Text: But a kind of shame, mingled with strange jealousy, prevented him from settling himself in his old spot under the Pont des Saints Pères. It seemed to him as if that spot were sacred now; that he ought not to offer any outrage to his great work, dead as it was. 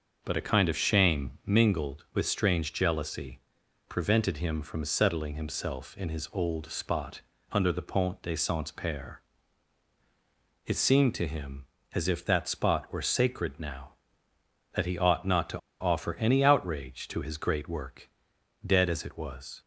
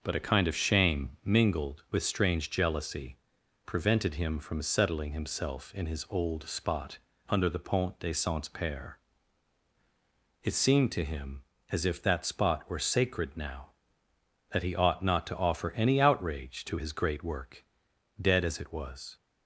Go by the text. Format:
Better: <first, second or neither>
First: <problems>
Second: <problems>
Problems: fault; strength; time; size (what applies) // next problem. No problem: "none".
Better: second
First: starts louder than the rest; until 1.2 s; 6 dB // pauses between "spot" and "under"; slight; at 7.2 s; 0.32 s long // pauses between "to" and "offer"; slight; at 15.5 s; 0.21 s long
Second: starts louder than the rest; until 1.0 s; 6 dB // pauses between "spot" and "under"; slight; at 6.9 s; 0.32 s long